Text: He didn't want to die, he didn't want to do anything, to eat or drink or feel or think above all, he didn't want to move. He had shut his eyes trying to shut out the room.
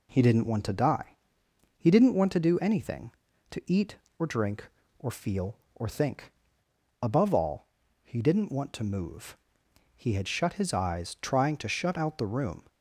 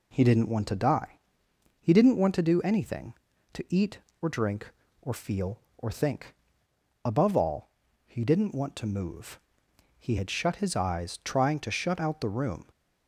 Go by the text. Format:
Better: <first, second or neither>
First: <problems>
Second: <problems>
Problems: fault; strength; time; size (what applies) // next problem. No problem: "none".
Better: neither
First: pauses between "think" and "above"; noticeable; at 6.3 s; 0.68 s long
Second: pauses between "think" and "above"; noticeable; at 6.3 s; 0.68 s long